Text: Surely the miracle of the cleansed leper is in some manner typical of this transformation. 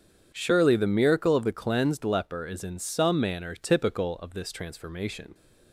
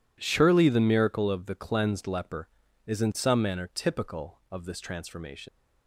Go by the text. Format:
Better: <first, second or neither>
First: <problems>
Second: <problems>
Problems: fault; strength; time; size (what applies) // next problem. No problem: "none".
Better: first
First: none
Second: leaves "transformation" unfinished; at 5.4 s; 80 ms